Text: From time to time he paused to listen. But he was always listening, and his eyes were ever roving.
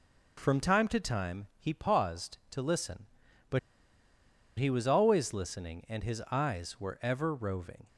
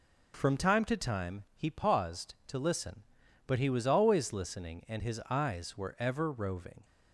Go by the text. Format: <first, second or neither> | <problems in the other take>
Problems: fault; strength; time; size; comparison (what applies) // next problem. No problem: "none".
second | pauses between "But" and "he"; at 3.5 s; 1.0 s long